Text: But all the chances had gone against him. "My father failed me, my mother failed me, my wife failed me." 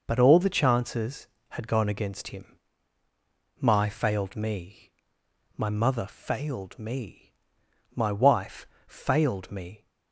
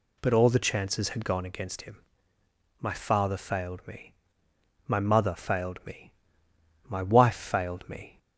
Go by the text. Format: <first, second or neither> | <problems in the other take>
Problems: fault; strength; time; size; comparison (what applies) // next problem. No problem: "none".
second | skips "father"; at 3.8 s // pauses between "wife" and "failed"; slight; at 8.6 s; 0.20 s long